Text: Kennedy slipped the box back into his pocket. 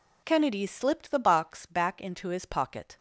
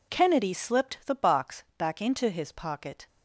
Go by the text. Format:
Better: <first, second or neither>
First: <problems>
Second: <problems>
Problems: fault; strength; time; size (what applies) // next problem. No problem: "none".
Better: neither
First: none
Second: none